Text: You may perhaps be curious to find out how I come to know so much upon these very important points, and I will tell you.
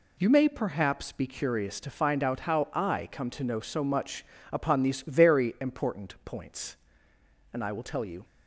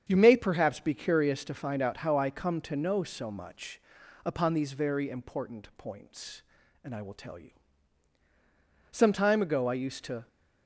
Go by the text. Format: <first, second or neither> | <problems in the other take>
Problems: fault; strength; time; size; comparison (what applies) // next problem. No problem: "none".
first | starts louder than the rest; strong; until 1.0 s; 7.5 dB // pauses between "much" and "upon"; noticeable; at 3.7 s; 0.46 s long; slight in the first // goes on to say "Some time ago I used to"; from 8.8 s on; 1.3 s long